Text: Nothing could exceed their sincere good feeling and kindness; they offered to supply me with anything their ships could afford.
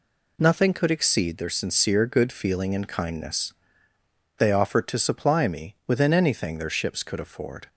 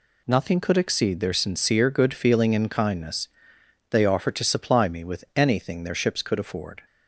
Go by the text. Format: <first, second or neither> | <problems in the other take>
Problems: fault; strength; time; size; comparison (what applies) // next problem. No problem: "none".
second | says "within" for "with"; at 5.8 s